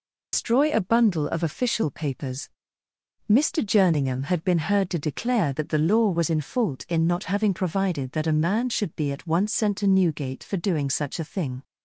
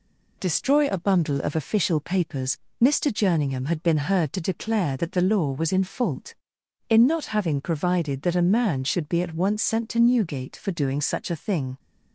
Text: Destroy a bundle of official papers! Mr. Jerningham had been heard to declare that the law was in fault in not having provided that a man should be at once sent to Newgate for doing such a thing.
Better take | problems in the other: second | loses the start of "Destroy"; at 0.3 s; 140 ms

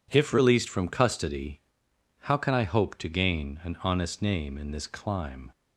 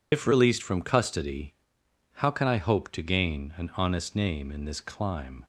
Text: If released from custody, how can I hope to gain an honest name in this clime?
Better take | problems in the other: first | loses the start of "If"; at 0.1 s; 100 ms

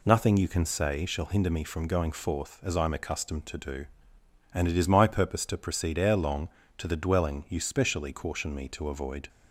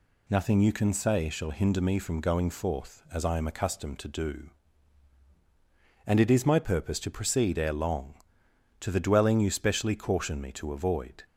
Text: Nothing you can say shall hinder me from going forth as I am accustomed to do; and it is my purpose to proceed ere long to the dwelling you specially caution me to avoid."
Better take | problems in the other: neither | none

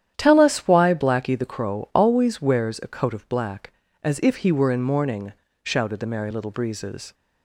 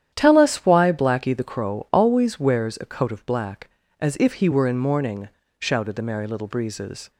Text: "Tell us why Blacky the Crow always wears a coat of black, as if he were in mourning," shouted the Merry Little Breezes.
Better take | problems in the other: neither | starts louder than the rest; strong; the same in both

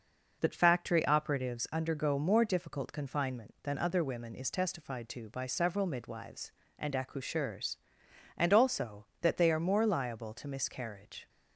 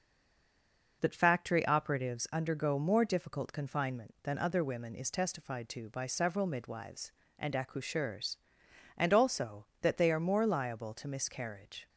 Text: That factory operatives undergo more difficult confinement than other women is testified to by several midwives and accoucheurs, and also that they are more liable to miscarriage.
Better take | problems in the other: first | stays silent before the first word; until 1.0 s; 1.0 s long

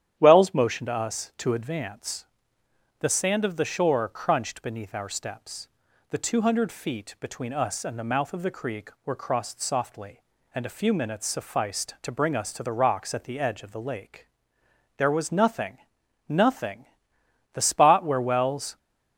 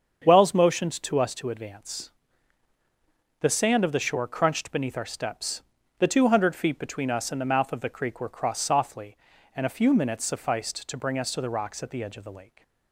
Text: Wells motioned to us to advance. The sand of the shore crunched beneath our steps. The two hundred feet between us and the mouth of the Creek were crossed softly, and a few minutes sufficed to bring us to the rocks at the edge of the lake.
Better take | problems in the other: second | starts louder than the rest; strong; until 1.2 s; 10.5 dB; strong in the second // goes on to say "There was nothing Nothing The spot where Wells"; strong; from 14.9 s on; 3.8 s long

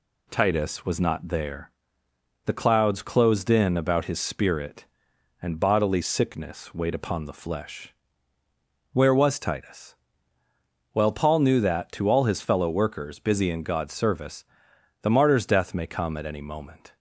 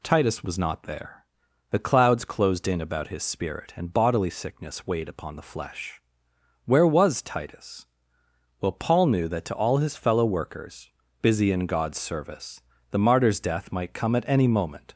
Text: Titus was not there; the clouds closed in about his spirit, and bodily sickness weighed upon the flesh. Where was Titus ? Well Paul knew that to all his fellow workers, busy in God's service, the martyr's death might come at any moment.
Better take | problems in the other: second | says "may" for "might"; at 15.7 s

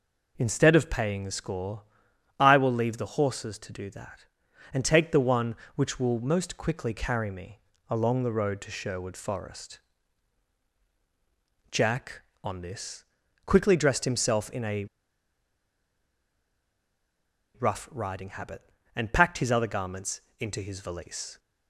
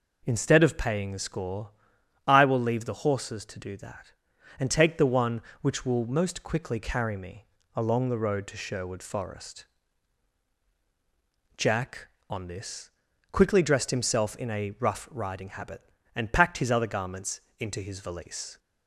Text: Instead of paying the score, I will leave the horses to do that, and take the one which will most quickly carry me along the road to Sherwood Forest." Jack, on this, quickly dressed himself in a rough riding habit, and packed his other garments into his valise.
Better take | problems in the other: second | pauses between "me" and "along"; slight; at 7.6 s; 0.28 s long; slight in the second // pauses between "a" and "rough"; strong; at 14.8 s; 2.7 s long // pauses between "garments" and "into"; slight; at 20.2 s; 0.18 s long; slight in the second

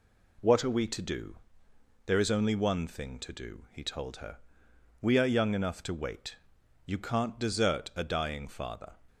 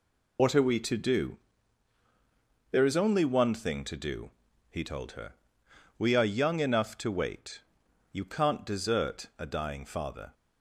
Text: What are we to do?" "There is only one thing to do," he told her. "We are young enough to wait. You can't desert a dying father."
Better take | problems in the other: first | loses the start of "What"; at 0.3 s; 55 ms

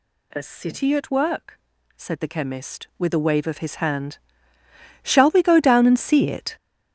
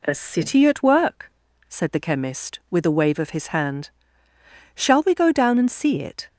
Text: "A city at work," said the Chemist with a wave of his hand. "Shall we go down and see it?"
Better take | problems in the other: second | gets louder; strong; throughout; 12.5 dB

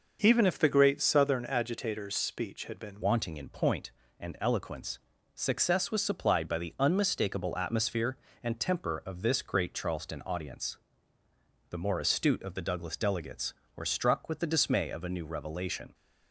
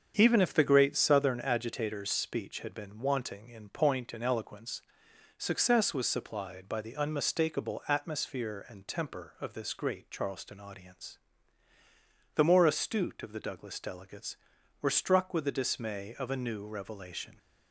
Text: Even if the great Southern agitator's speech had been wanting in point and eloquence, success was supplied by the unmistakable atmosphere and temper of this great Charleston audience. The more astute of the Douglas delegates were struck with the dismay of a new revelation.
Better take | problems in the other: second | starts louder than the rest; noticeable; until 1.2 s; 6 dB; strong in the second // changes voice at "wanting"; from 3.0 s on; 12.9 s long

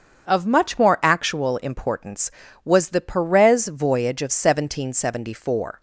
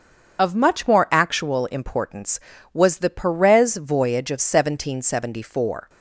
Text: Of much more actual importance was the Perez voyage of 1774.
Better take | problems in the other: first | loses the start of "Of"; at 0.3 s; 45 ms // starts louder than the rest; until 1.4 s; 7 dB; also in the first

